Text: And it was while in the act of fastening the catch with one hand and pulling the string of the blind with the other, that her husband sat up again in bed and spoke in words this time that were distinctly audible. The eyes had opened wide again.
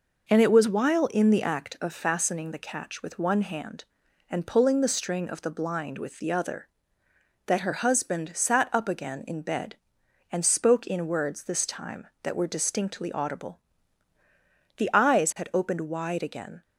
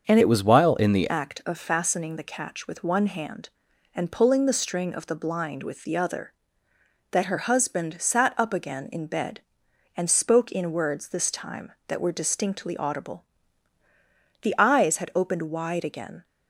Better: first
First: none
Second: starts louder than the rest; until 1.1 s; 6.5 dB // changes voice from "it" to "the"; from 0.1 to 1.0 s; 0.9 s long

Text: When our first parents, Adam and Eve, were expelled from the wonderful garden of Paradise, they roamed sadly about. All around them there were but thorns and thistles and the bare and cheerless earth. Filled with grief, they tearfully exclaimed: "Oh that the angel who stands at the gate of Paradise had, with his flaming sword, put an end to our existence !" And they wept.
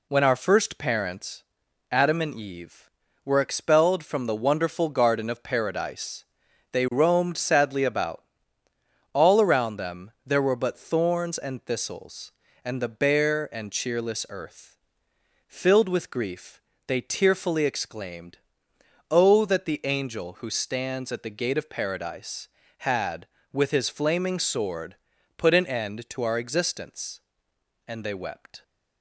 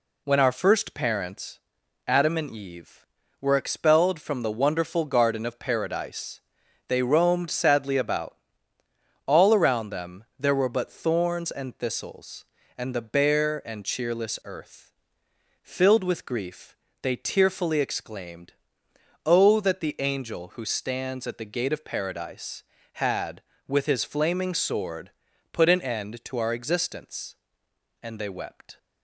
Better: neither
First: pauses between "them" and "there"; slight; at 10.1 s; 0.16 s long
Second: pauses between "them" and "there"; slight; at 10.2 s; 0.16 s long

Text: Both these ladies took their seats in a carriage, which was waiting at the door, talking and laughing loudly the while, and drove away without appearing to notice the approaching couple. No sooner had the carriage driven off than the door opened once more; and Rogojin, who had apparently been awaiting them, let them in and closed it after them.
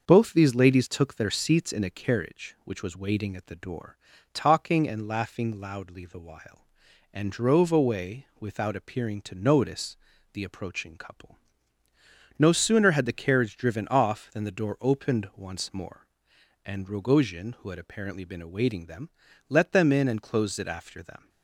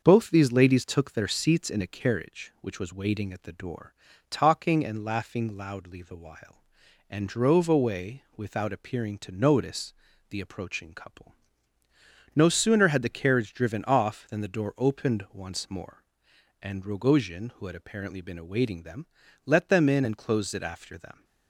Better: neither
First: starts louder than the rest; until 1.0 s; 6.5 dB // pauses between "notice" and "the"; slight; at 9.9 s; 0.36 s long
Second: starts louder than the rest; until 1.0 s; 6.5 dB // pauses between "notice" and "the"; slight; at 9.9 s; 0.36 s long

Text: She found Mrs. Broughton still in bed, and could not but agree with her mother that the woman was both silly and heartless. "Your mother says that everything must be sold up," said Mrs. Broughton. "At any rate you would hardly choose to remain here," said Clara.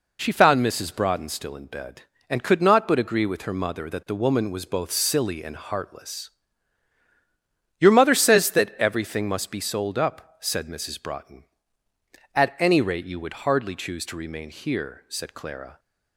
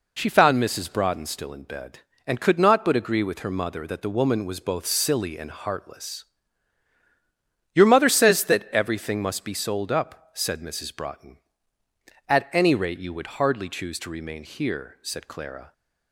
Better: neither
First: none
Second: none

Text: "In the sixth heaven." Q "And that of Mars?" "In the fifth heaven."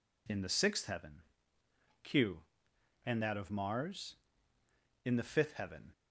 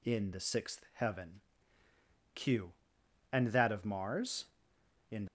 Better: first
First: none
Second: stops before "the fifth heaven"; at 5.2 s

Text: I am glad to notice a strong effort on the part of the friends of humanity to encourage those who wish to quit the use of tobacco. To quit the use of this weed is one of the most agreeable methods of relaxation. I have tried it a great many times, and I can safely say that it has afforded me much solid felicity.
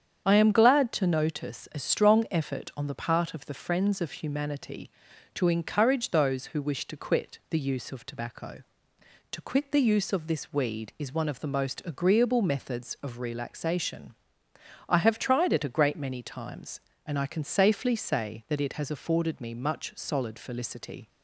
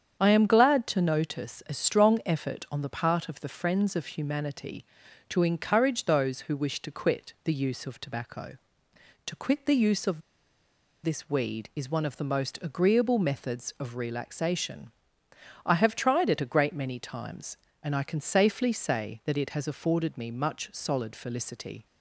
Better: first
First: starts louder than the rest; strong; until 1.2 s; 8 dB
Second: starts louder than the rest; strong; until 1.2 s; 8 dB // pauses between "of" and "this"; noticeable; at 10.2 s; 0.83 s long

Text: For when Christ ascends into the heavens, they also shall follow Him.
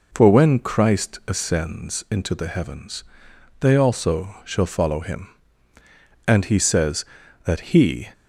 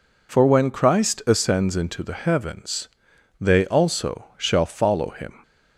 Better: second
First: goes on to say "And He says that He"; strong; from 6.2 s on; 1.8 s long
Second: none

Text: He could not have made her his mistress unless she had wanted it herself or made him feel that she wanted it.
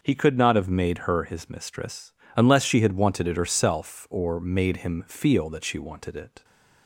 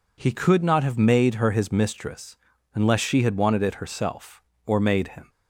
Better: first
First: pauses between "mistress" and "unless"; slight; at 2.1 s; 0.24 s long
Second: pauses between "mistress" and "unless"; at 2.3 s; 0.40 s long // stops before "feel that she wanted it"; at 5.2 s

